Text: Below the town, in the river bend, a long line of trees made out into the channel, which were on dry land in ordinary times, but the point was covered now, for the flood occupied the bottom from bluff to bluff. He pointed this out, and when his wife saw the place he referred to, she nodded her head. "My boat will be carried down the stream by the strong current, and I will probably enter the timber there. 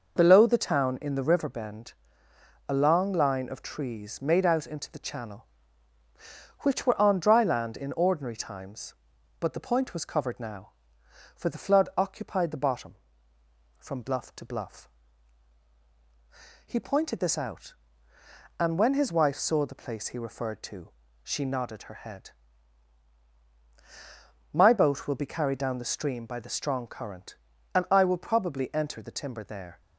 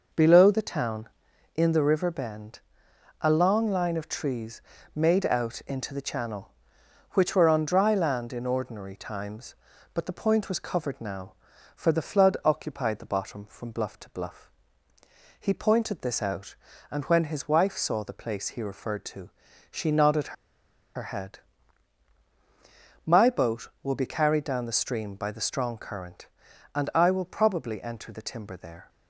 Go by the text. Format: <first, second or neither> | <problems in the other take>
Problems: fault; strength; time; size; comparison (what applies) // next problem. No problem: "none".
first | pauses between "trees" and "made"; slight; at 4.5 s; 0.34 s long // pauses between "nodded" and "her"; noticeable; at 20.3 s; 0.61 s long